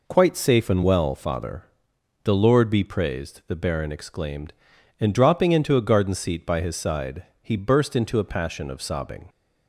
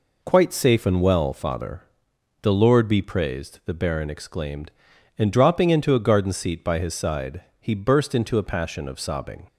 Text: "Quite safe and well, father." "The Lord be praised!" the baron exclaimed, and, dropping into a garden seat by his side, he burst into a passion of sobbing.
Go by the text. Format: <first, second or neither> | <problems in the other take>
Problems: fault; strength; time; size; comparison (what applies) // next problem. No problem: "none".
neither | none